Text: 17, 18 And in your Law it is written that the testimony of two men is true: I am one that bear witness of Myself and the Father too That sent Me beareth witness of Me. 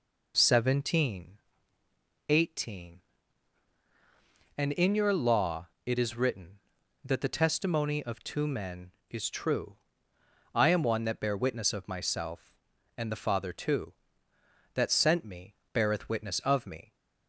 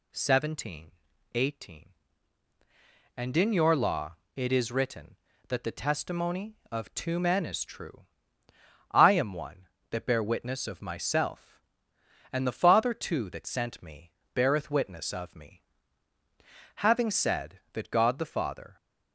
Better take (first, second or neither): first